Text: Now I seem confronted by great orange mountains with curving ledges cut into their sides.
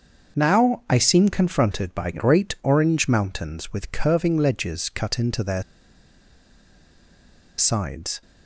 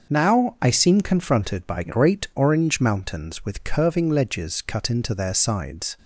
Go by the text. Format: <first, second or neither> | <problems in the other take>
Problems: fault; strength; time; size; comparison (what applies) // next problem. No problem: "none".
second | starts louder than the rest; until 1.4 s; 6.5 dB; also in the second // pauses between "their" and "sides"; strong; at 5.6 s; 1.9 s long